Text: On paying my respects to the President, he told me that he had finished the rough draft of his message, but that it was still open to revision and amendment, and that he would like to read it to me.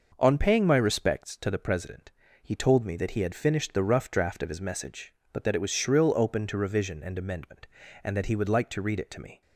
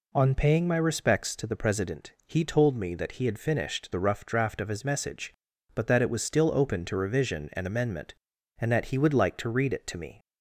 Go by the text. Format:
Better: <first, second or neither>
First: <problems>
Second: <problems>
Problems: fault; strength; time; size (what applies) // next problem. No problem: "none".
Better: second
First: says "shrill" for "still"; at 5.7 s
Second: none